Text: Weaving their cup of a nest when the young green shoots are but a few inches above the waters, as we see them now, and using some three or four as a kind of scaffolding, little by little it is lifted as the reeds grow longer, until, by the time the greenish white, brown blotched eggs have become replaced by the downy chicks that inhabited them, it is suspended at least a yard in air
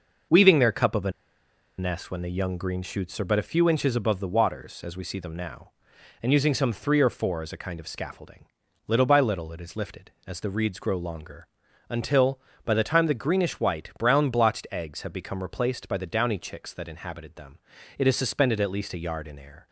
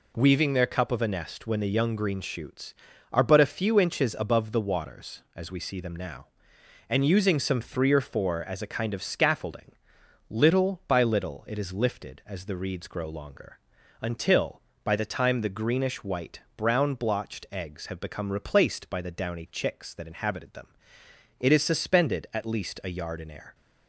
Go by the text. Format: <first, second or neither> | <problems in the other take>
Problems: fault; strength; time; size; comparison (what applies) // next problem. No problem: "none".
second | pauses between "a" and "nest"; noticeable; at 1.1 s; 0.67 s long